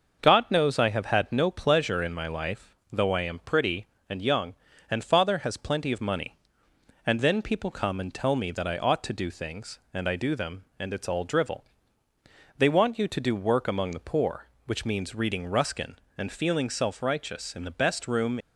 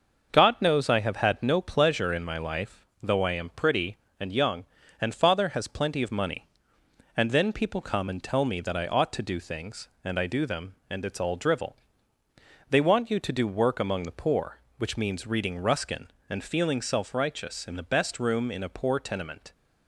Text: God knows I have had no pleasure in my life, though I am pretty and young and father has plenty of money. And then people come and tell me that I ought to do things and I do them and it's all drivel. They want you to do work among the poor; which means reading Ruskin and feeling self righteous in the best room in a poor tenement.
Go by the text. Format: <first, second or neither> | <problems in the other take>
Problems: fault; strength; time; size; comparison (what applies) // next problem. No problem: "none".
second | starts louder than the rest; until 1.2 s; 6 dB; also in the second // stops before "in a poor tenement"; at 18.3 s